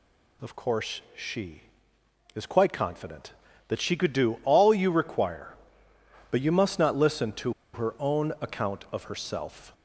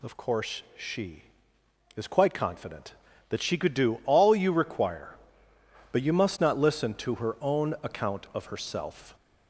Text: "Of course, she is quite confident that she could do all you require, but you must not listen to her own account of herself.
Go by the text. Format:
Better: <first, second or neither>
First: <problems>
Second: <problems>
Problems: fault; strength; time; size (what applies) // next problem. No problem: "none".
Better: second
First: pauses between "to" and "her"; slight; at 7.5 s; 0.20 s long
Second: none